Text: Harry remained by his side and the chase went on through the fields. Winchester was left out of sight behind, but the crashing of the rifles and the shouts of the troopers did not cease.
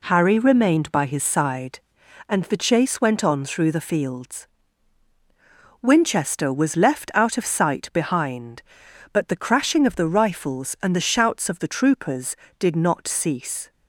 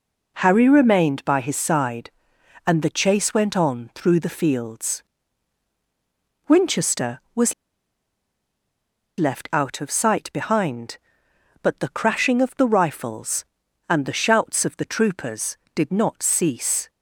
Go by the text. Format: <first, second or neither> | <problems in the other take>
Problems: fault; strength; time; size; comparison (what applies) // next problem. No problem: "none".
first | pauses between "was" and "left"; strong; at 7.5 s; 1.6 s long